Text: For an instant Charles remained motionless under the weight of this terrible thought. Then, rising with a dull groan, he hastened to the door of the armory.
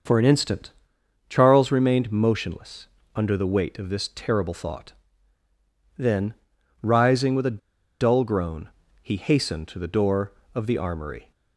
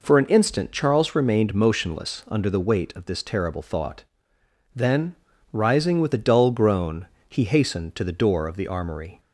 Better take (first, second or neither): second